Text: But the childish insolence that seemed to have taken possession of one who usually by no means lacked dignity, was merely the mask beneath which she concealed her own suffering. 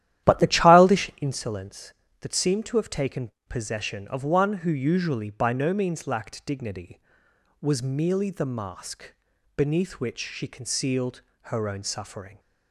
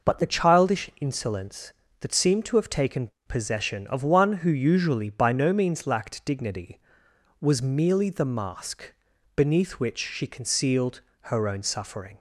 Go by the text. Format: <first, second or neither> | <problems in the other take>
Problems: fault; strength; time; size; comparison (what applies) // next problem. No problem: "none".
second | starts louder than the rest; strong; until 1.4 s; 12.5 dB // pauses between "taken" and "possession"; slight; at 3.2 s; 0.20 s long; slight in the second // pauses between "mask" and "beneath"; at 9.1 s; 0.42 s long; also in the second // pauses between "concealed" and "her"; slight; at 11.2 s; 0.22 s long; slight in the second